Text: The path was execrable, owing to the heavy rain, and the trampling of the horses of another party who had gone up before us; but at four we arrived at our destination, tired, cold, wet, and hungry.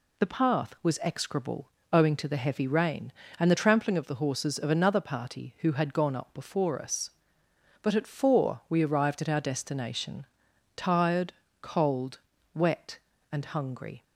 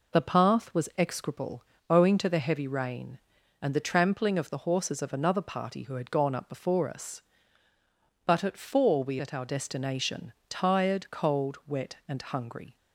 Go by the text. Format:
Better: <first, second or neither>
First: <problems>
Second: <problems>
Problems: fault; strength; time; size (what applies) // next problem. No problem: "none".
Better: first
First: none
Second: skips "arrived"; at 9.2 s